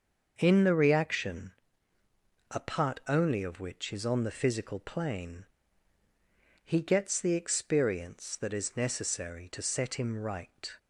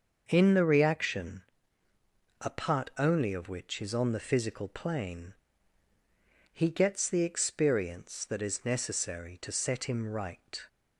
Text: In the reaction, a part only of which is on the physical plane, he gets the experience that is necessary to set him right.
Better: neither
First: starts louder than the rest; until 1.3 s; 6.5 dB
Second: starts louder than the rest; until 1.2 s; 6.5 dB

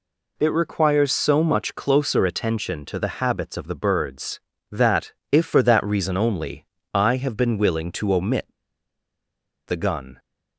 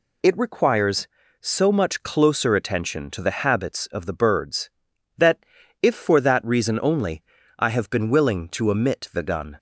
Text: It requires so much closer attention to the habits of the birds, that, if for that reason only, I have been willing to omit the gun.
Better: second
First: pauses between "omit" and "the"; at 8.4 s; 1.2 s long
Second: none

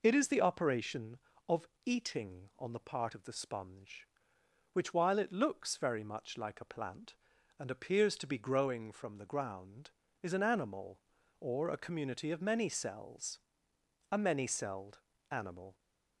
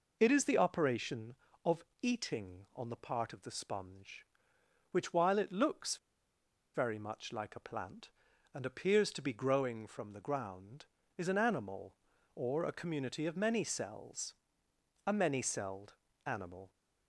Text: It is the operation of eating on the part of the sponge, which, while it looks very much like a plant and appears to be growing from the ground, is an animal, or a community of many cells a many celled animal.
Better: first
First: pauses between "of" and "eating"; slight; at 1.6 s; 0.18 s long // pauses between "cells" and "a"; noticeable; at 13.3 s; 0.72 s long // pauses between "celled" and "animal"; slight; at 14.9 s; 0.32 s long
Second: pauses between "of" and "eating"; slight; at 1.8 s; 0.18 s long // pauses between "looks" and "very"; noticeable; at 5.9 s; 0.78 s long // pauses between "cells" and "a"; noticeable; at 14.3 s; 0.72 s long // pauses between "celled" and "animal"; slight; at 15.9 s; 0.32 s long

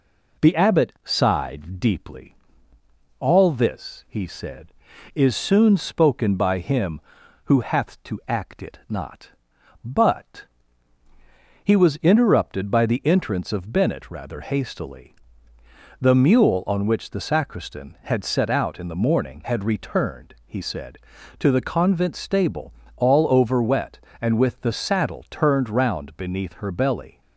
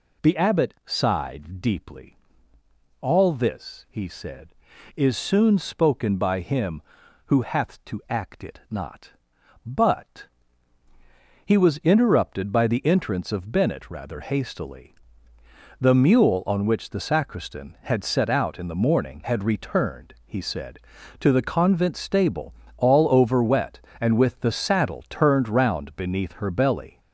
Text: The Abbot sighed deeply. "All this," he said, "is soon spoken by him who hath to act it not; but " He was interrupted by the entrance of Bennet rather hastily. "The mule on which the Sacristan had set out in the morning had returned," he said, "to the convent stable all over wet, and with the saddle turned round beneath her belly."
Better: first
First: pauses between "stable" and "all"; slight; at 22.7 s; 0.22 s long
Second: gets louder; noticeable; throughout; 6 dB // pauses between "stable" and "all"; slight; at 22.5 s; 0.22 s long

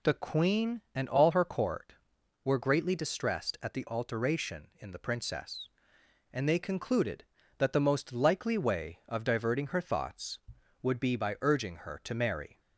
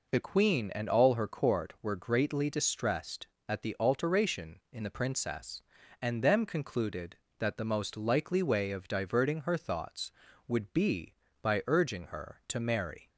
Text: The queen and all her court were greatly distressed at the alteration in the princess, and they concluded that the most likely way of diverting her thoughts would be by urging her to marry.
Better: first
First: none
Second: says "them" for "they"; at 6.2 s

